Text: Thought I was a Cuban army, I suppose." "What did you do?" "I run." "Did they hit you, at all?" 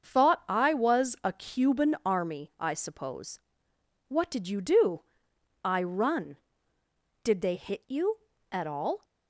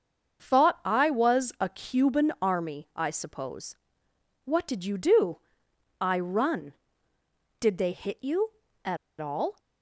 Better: first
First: starts louder than the rest; until 1.0 s; 6.5 dB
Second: starts louder than the rest; until 1.4 s; 6.5 dB // pauses between "at" and "all"; slight; at 8.9 s; 0.23 s long

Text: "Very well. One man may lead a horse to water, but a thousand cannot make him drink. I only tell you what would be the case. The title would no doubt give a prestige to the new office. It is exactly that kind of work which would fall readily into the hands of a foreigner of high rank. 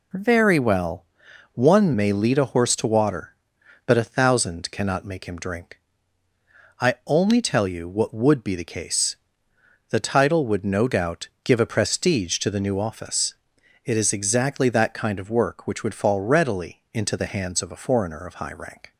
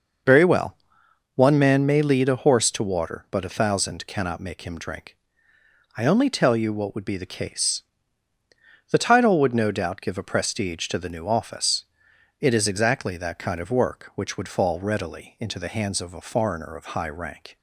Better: second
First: skips "man"; at 1.9 s // pauses between "doubt" and "give"; slight; at 11.2 s; 0.16 s long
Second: none

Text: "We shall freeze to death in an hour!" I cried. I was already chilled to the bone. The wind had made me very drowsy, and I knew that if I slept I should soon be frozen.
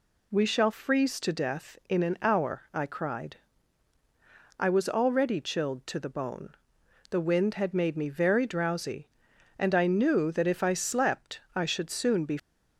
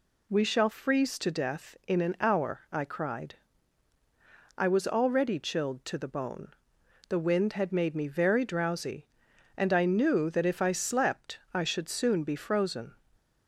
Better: second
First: stops before "frozen"; at 12.3 s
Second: none

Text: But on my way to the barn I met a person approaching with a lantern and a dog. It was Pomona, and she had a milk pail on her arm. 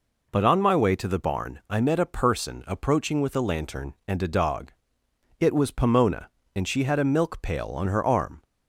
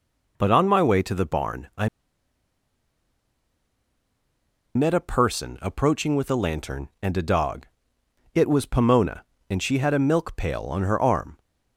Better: first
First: none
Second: pauses between "I" and "met"; strong; at 1.8 s; 2.8 s long

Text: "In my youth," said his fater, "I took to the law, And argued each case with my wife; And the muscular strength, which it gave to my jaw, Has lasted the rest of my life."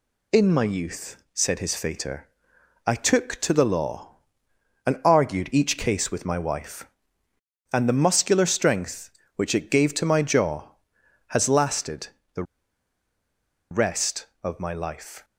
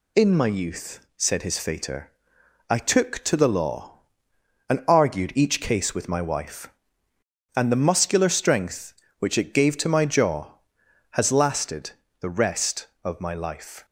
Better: second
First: pauses between "lasted" and "the"; slight; at 12.0 s; 0.24 s long // pauses between "the" and "rest"; strong; at 12.4 s; 1.2 s long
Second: pauses between "lasted" and "the"; slight; at 11.9 s; 0.26 s long

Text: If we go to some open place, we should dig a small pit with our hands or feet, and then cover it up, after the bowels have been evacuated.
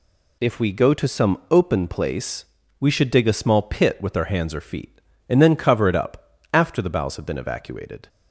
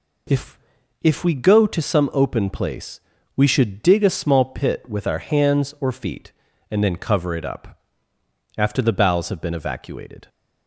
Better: first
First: none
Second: says "If" twice; at 1.0 s

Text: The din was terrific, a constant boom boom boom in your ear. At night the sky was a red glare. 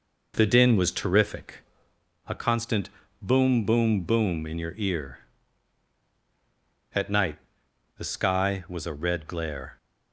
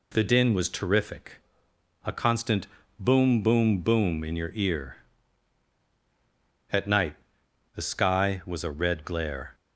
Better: second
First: starts louder than the rest; noticeable; until 2.0 s; 5 dB // pauses between "constant" and "boom"; slight; at 2.8 s; 0.32 s long // pauses between "night" and "the"; noticeable; at 7.3 s; 0.58 s long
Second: pauses between "constant" and "boom"; slight; at 2.6 s; 0.32 s long // pauses between "night" and "the"; noticeable; at 7.1 s; 0.58 s long

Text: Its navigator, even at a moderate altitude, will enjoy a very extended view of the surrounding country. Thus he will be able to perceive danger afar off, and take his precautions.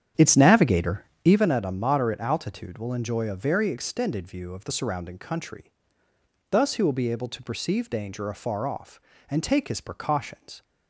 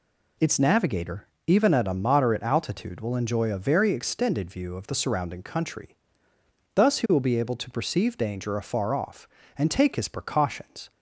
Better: second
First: starts louder than the rest; strong; until 1.5 s; 9 dB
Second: none

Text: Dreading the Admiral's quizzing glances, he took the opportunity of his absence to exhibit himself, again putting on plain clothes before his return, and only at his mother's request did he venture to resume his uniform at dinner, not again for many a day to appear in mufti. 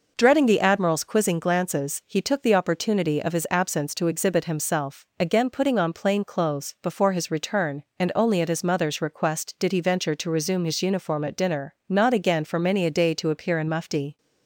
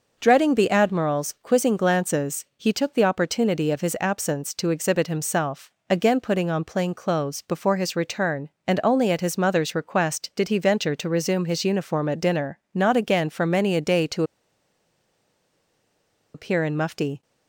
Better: first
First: none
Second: pauses between "to" and "appear"; strong; at 14.2 s; 2.1 s long

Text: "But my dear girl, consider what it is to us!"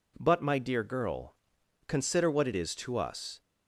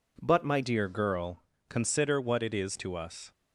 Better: first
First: none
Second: changes voice at "dear"; from 0.6 s on; 2.7 s long

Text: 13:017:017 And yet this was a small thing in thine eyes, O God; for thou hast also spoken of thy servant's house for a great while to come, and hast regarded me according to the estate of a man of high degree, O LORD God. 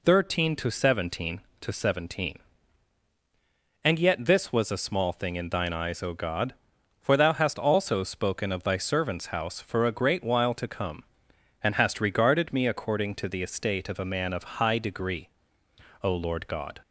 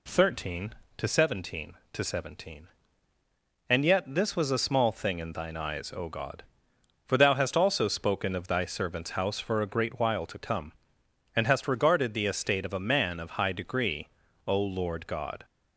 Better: first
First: none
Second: skips "me according to"; at 12.1 s

